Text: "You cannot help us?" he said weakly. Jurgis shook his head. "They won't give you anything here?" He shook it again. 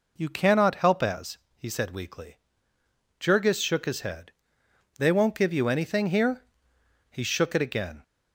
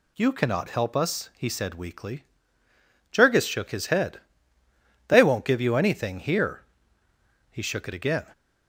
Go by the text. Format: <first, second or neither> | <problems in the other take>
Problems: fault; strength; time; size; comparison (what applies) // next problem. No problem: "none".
second | says "as" for "us"; at 1.0 s